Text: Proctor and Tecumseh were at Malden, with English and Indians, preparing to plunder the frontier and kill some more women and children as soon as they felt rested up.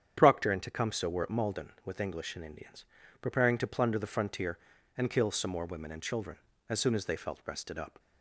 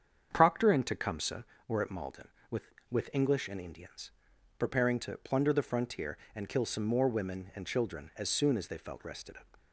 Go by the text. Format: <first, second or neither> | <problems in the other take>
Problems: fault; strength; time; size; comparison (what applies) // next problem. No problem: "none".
first | starts louder than the rest; strong; until 1.3 s; 7.5 dB; strong in the first // says "with" twice; at 2.8 s